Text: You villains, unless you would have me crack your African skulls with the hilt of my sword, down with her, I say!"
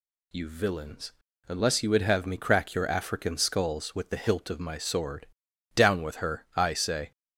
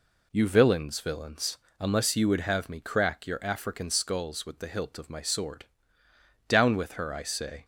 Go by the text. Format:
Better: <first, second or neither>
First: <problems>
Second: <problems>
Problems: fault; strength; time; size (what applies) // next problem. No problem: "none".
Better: first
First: none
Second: says "villains" twice; at 1.0 s